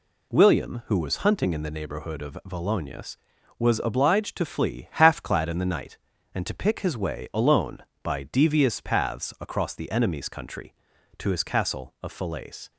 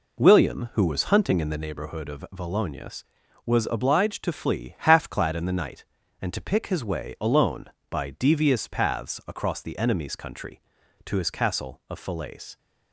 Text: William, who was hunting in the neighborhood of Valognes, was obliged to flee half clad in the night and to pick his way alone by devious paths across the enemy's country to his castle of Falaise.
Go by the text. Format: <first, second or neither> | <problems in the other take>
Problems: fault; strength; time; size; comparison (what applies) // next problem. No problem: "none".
first | starts louder than the rest; until 1.7 s; 3.5 dB